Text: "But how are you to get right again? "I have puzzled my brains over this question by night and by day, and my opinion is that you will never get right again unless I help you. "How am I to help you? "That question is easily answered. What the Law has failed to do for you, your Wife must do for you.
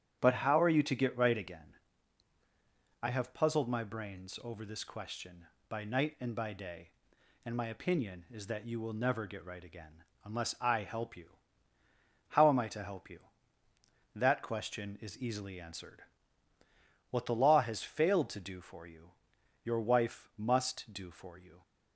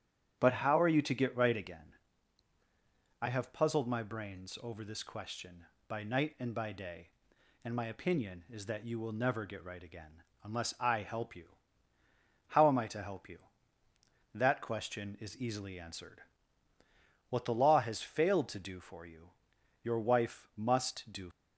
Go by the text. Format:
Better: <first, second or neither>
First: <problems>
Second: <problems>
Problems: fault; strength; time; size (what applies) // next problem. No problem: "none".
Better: first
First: starts louder than the rest; strong; until 1.2 s; 9.5 dB // pauses between "again" and "unless"; slight; at 10.0 s; 0.22 s long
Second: starts louder than the rest; strong; until 1.4 s; 9.5 dB // pauses between "again" and "unless"; slight; at 10.2 s; 0.22 s long // stops before "for you"; at 21.3 s